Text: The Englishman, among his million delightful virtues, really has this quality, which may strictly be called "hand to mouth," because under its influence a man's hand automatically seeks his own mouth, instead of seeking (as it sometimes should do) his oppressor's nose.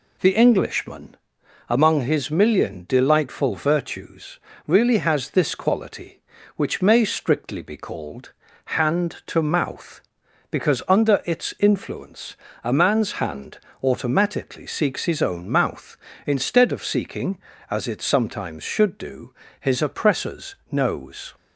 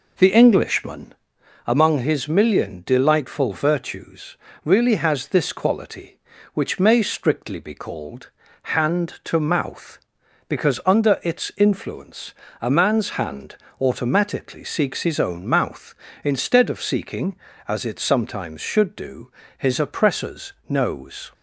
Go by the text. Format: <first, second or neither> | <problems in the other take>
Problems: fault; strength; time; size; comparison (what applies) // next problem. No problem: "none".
first | starts louder than the rest; noticeable; until 1.4 s; 4.5 dB // pauses between "called" and "hand"; slight; at 8.2 s; 0.32 s long; slight in the first // pauses between "influence" and "a"; slight; at 12.3 s; 0.28 s long; slight in the first // pauses between "hand" and "automatically"; slight; at 13.5 s; 0.24 s long; slight in the first // pauses between "oppressor's" and "nose"; slight; at 20.5 s; 0.16 s long; slight in the first